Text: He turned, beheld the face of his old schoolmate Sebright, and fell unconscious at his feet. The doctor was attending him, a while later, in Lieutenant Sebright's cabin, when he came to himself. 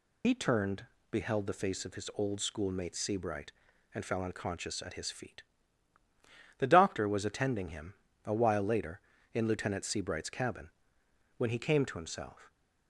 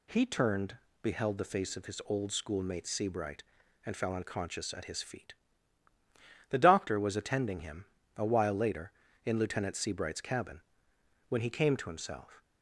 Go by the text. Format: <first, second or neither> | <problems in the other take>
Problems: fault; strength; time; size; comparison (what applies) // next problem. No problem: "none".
second | loses the start of "He"; at 0.2 s; 70 ms